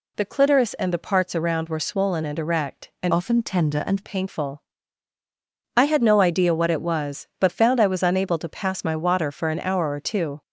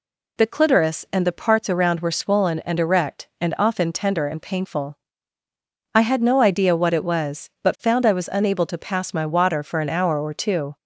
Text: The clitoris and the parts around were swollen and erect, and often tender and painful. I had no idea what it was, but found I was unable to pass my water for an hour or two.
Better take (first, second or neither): second